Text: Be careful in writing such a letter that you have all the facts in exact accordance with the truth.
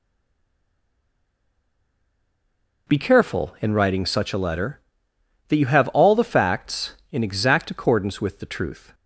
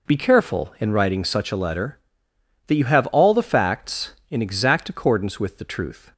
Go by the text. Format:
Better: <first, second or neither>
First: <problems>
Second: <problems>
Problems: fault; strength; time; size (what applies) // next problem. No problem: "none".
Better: second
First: stays silent before the first word; strong; until 2.8 s; 2.8 s long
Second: none